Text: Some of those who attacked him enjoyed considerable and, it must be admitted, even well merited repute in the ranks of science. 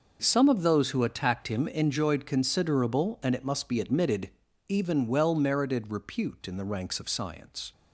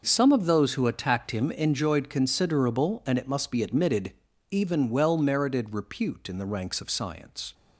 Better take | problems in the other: neither | none

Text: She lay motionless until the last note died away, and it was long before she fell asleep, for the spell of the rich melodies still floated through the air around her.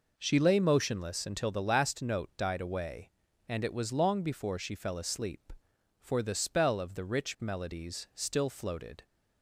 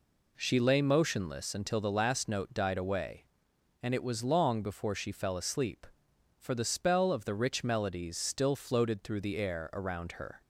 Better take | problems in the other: second | stops before "through the air around her"; at 9.0 s

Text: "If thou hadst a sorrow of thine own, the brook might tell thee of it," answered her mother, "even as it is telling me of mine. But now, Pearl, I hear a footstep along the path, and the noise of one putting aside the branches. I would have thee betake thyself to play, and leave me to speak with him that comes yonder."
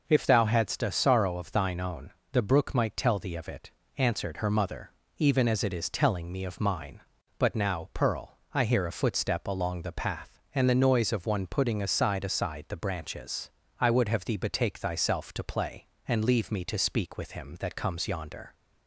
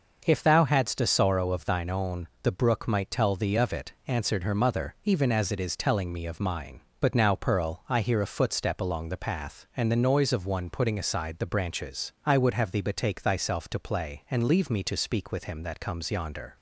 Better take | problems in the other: second | says "aside" twice; at 12.2 s

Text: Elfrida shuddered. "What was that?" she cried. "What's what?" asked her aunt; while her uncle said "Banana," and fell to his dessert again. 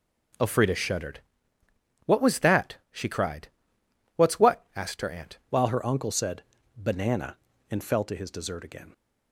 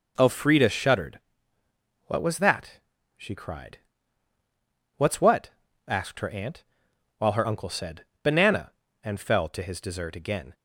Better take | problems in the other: second | changes voice at "while"; from 5.4 s on; 3.5 s long // pauses between "said" and "Banana"; slight; at 6.4 s; 0.34 s long; slight in the second

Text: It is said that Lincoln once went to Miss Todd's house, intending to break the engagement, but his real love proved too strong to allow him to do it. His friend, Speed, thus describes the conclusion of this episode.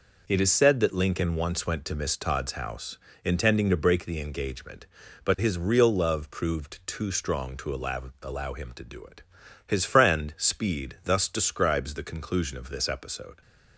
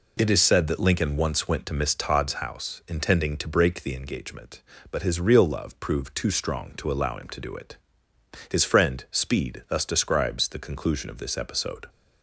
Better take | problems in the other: second | says "allow" twice; at 8.2 s

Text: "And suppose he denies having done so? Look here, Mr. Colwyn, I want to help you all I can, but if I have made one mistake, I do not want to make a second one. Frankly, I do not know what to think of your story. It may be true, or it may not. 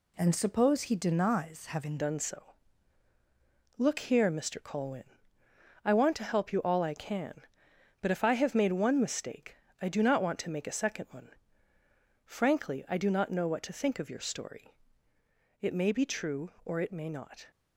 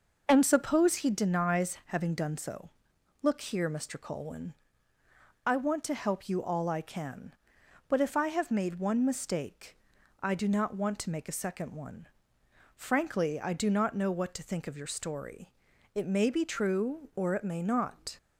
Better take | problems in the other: second | changes voice at "done"; from 1.9 s on; 15.5 s long

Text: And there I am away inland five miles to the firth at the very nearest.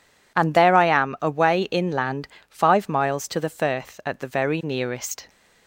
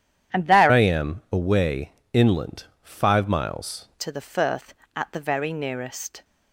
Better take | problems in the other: first | starts louder than the rest; strong; until 1.4 s; 10 dB // changes voice from "I" to "miles"; from 0.6 to 3.8 s; 3.2 s long // pauses between "away" and "inland"; slight; at 1.9 s; 0.20 s long // pauses between "inland" and "five"; slight; at 2.6 s; 0.16 s long; slight in the first

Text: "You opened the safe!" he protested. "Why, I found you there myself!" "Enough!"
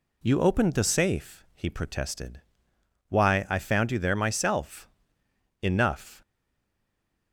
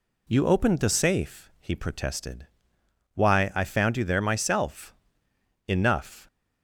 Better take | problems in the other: second | stays silent after the last word; from 6.2 s on; 1.1 s long

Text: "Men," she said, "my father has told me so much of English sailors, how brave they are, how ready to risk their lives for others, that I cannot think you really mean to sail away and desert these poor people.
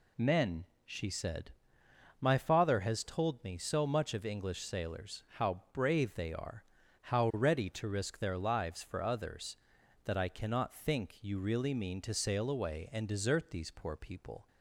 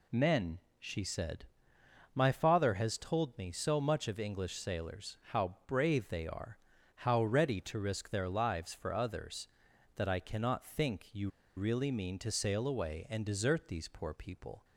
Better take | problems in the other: first | pauses between "you" and "really"; slight; at 11.2 s; 0.28 s long

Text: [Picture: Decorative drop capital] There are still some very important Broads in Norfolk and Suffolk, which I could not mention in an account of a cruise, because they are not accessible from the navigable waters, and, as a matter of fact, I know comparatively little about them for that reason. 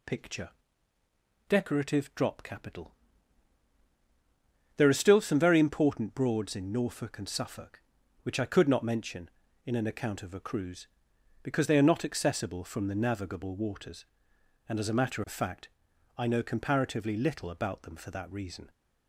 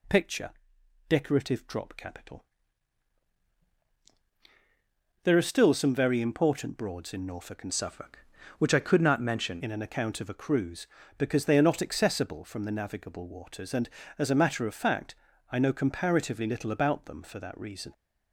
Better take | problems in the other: first | pauses between "capital" and "There"; strong; at 2.4 s; 2.8 s long; strong in the first // changes voice from "Suffolk" to "mention"; from 7.7 to 9.6 s; 1.9 s long

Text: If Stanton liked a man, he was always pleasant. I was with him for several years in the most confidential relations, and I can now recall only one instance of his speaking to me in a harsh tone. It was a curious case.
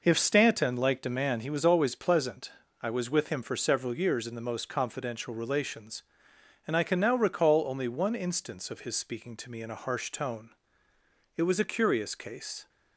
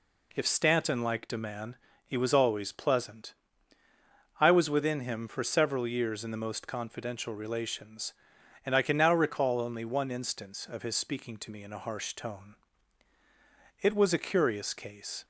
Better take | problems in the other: first | says "within" for "with"; at 4.6 s

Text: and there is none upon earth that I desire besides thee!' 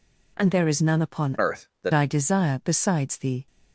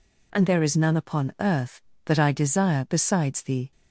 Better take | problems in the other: second | changes voice from "earth" to "that"; from 1.3 to 1.9 s; 0.6 s long

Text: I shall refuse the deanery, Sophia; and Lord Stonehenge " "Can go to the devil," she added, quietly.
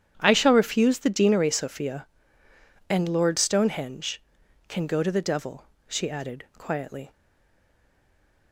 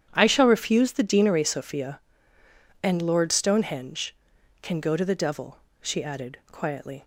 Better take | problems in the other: second | starts louder than the rest; strong; until 1.2 s; 10 dB; strong in the second // stays silent after the last word; noticeable; from 7.1 s on; 1.4 s long

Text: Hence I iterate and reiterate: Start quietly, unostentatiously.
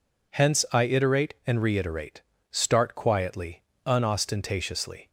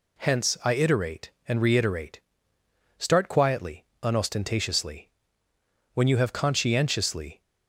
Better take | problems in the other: first | goes on to say "When you have conscientiously"; from 5.9 s on; 1.4 s long

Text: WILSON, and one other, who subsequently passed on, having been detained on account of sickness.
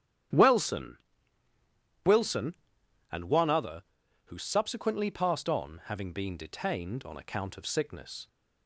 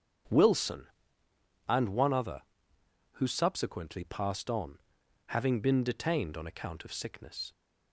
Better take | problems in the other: second | starts louder than the rest; strong; until 2.4 s; 11 dB; strong in the second // says "WILSON" twice; at 2.0 s

